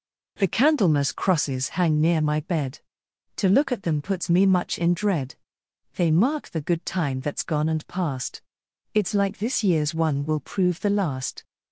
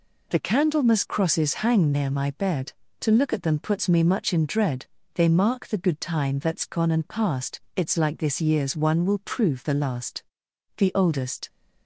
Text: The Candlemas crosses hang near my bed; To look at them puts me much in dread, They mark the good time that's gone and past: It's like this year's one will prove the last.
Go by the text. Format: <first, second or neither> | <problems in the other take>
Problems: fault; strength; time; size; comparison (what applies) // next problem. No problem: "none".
first | goes on to say "The oldest"; noticeable; from 10.7 s on; 0.72 s long